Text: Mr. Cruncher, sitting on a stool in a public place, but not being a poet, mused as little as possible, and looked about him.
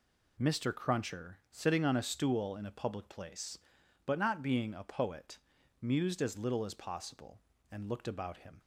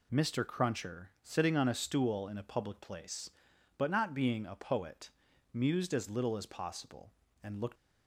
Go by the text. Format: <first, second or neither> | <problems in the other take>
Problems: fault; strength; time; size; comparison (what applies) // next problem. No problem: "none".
first | stops before "about him"; at 7.7 s